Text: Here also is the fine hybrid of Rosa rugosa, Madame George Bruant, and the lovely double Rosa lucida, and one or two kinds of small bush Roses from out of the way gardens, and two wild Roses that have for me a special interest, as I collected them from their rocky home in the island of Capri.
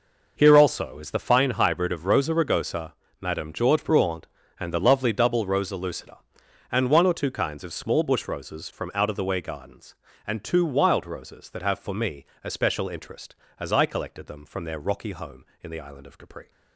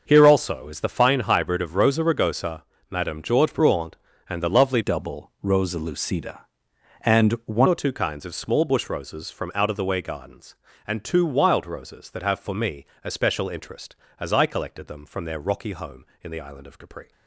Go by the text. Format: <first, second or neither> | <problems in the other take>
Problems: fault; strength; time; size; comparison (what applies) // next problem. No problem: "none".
first | starts louder than the rest; noticeable; until 1.0 s; 6 dB // changes voice from "double" to "one"; from 4.8 to 7.6 s; 2.8 s long // pauses between "me" and "a"; slight; at 12.8 s; 0.20 s long; slight in the first